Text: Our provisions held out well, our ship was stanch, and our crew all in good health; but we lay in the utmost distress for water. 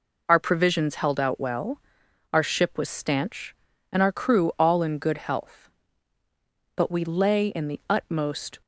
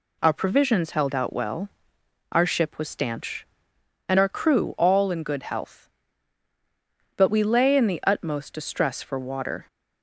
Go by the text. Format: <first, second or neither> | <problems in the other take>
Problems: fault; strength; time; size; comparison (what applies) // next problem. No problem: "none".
second | stops before "distress for water"; at 8.6 s